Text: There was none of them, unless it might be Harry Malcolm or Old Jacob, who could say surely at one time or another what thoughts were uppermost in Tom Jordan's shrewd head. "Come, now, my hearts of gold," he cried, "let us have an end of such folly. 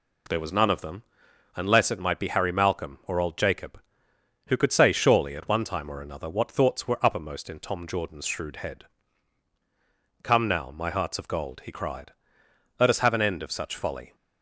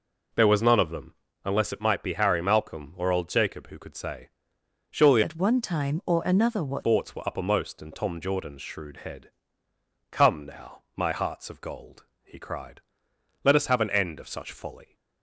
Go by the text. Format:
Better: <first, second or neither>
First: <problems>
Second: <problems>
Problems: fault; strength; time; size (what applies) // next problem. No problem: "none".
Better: first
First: none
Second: pauses between "say" and "surely"; noticeable; at 4.2 s; 0.64 s long // changes voice from "at" to "what"; from 5.2 to 6.8 s; 1.6 s long